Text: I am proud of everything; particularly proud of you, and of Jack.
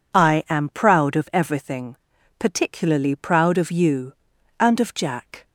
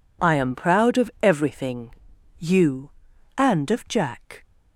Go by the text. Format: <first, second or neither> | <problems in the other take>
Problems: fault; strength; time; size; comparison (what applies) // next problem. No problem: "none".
first | skips "particularly proud of"; at 2.1 s